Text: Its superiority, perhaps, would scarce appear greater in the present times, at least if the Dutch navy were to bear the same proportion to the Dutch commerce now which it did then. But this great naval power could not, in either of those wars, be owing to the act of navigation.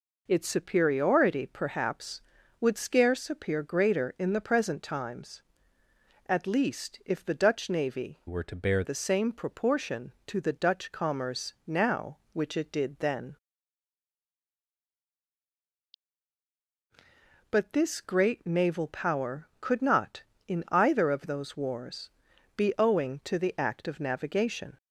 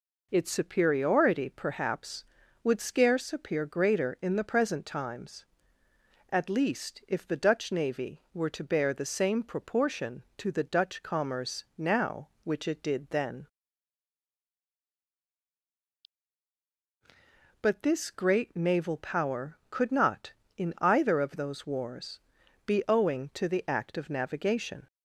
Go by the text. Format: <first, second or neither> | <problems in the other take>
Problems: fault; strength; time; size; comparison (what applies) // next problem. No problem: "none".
second | changes voice from "were" to "bear"; from 8.2 to 8.8 s; 0.6 s long